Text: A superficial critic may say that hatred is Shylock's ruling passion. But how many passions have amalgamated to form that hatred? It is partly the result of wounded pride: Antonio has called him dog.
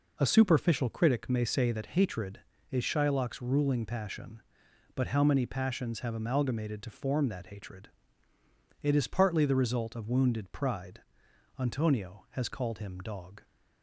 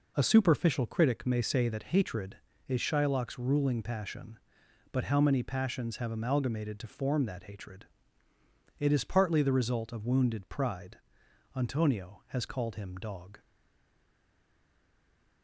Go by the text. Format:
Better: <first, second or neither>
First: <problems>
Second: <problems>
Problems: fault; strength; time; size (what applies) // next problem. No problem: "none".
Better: first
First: none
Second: stays silent after the last word; noticeable; from 13.4 s on; 2.0 s long